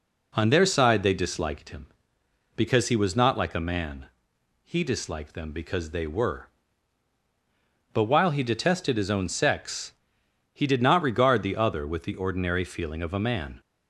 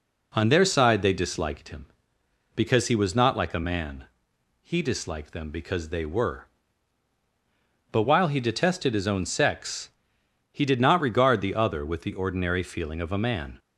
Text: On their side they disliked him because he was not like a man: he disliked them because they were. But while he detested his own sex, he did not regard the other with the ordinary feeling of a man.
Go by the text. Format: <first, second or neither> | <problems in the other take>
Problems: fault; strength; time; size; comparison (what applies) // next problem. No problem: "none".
neither | none